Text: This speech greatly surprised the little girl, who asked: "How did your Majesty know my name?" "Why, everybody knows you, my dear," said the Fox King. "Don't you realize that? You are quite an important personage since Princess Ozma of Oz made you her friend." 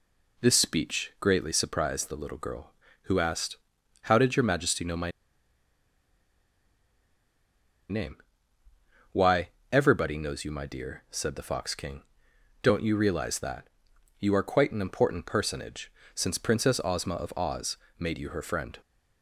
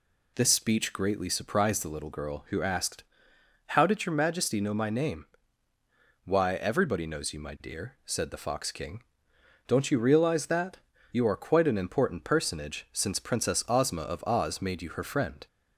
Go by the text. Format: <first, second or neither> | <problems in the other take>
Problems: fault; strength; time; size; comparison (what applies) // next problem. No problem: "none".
second | pauses between "my" and "name"; strong; at 5.0 s; 2.8 s long // pauses between "personage" and "since"; slight; at 15.8 s; 0.24 s long // pauses between "Oz" and "made"; slight; at 17.7 s; 0.20 s long